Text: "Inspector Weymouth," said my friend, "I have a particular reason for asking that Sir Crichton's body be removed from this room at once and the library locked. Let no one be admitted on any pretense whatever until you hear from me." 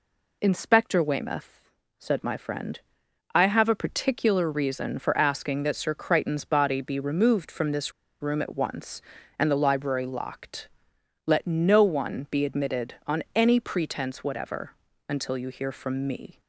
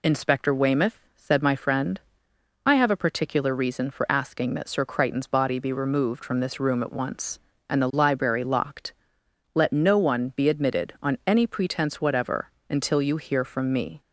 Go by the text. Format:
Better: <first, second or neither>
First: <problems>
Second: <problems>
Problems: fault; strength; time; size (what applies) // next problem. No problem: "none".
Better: second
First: pauses between "this" and "room"; slight; at 7.9 s; 0.29 s long // pauses between "whatever" and "until"; slight; at 14.7 s; 0.36 s long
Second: pauses between "whatever" and "until"; slight; at 12.5 s; 0.18 s long